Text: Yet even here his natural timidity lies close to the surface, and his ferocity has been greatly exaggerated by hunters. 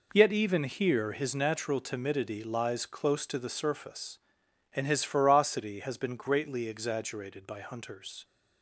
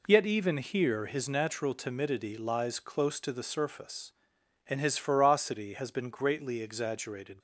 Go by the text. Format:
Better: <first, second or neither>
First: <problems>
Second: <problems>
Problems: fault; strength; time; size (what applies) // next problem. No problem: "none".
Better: first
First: none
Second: stops before "by hunters"; at 7.3 s